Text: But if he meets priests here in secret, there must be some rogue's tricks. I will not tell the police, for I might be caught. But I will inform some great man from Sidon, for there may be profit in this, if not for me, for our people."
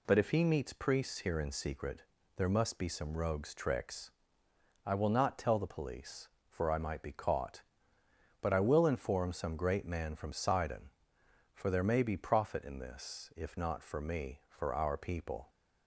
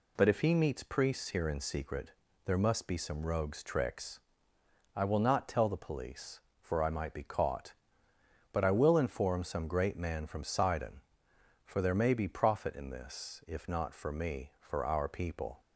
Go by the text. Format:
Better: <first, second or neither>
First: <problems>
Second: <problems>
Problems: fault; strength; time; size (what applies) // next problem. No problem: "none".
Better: neither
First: none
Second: none